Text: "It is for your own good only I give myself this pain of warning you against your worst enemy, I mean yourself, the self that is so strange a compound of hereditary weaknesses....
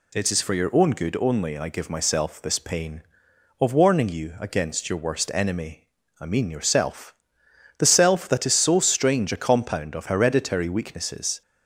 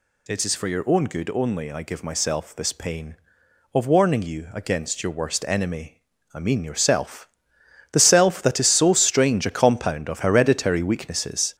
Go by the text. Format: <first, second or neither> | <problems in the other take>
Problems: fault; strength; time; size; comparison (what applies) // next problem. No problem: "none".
first | gets louder; noticeable; throughout; 6 dB